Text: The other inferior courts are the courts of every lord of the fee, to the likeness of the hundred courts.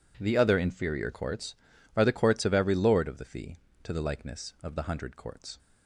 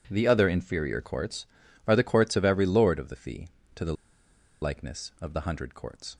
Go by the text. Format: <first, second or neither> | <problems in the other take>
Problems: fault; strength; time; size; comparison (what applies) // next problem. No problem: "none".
first | pauses between "the" and "likeness"; noticeable; at 3.9 s; 0.68 s long